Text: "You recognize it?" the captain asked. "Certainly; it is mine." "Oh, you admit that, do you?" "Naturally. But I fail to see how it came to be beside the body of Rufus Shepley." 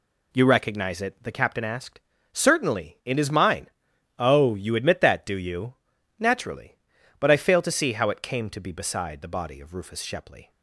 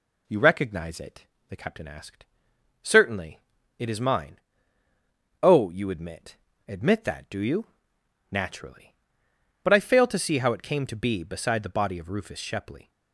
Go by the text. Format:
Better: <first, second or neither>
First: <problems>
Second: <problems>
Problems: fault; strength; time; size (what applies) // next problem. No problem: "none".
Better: first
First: none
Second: says "admit" twice; at 6.6 s